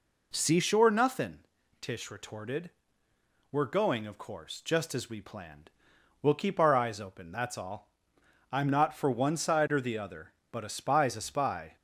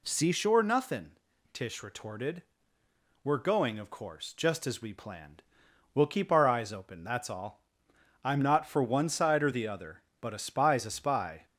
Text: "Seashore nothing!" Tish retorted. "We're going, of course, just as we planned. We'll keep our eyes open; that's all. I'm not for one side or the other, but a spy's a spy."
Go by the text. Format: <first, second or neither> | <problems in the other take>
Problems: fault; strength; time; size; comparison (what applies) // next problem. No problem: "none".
second | starts louder than the rest; noticeable; until 1.6 s; 4 dB